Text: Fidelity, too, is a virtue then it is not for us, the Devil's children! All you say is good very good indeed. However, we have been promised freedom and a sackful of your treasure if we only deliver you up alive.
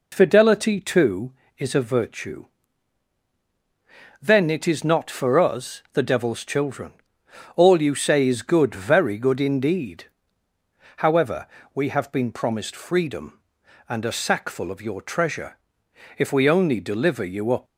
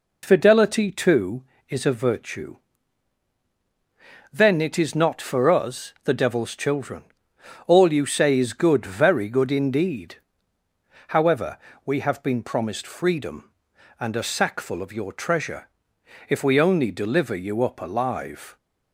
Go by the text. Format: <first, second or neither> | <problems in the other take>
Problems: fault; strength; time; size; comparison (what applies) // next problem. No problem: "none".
second | pauses between "virtue" and "then"; strong; at 2.4 s; 1.7 s long; strong in the second // pauses between "treasure" and "if"; noticeable; at 15.5 s; 0.60 s long; noticeable in the second // stops before "alive"; at 17.6 s